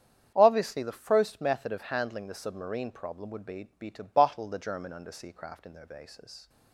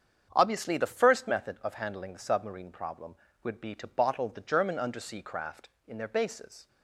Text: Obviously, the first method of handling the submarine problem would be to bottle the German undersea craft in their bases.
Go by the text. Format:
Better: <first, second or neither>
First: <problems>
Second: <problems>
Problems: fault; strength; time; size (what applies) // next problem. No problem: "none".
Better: second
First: starts louder than the rest; strong; until 1.3 s; 8 dB // says "be" twice; at 3.7 s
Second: starts louder than the rest; strong; until 1.3 s; 7.5 dB